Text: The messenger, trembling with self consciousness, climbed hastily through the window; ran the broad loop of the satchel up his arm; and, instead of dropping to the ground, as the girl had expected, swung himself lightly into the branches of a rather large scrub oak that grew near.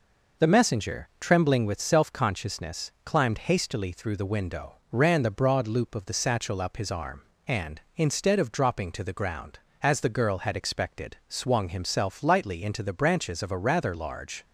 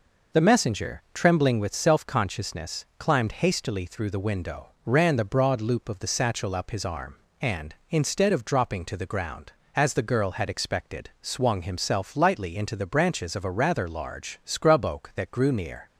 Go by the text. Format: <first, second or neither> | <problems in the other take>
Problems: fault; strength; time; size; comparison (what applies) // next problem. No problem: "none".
second | stops before "scrub oak that grew near"; at 14.4 s